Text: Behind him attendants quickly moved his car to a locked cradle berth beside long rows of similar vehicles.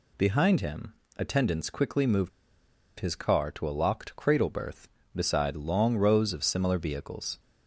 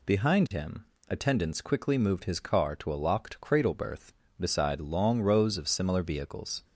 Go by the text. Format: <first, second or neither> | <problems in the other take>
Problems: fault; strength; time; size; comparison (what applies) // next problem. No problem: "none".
second | pauses between "him" and "attendants"; slight; at 0.9 s; 0.24 s long; slight in the second // pauses between "moved" and "his"; noticeable; at 2.2 s; 0.69 s long